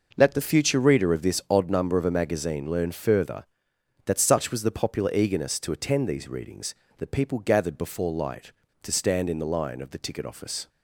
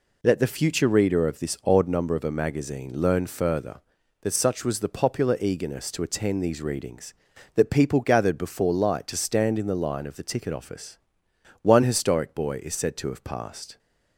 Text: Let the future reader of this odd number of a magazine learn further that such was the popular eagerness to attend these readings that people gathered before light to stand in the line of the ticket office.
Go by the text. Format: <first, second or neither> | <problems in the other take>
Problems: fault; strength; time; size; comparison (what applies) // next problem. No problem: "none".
first | goes on to say "One historic boy is said to have passed"; strong; from 11.6 s on; 2.1 s long